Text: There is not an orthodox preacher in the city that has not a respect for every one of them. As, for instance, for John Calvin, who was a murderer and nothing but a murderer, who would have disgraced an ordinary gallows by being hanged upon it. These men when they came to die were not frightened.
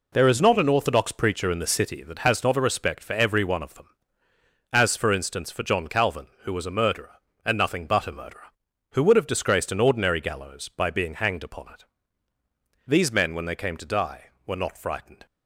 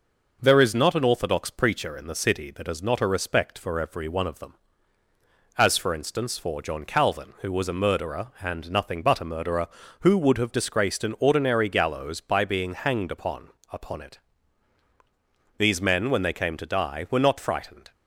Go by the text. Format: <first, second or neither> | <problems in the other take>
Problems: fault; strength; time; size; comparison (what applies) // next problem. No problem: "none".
first | says "upon" twice; at 13.7 s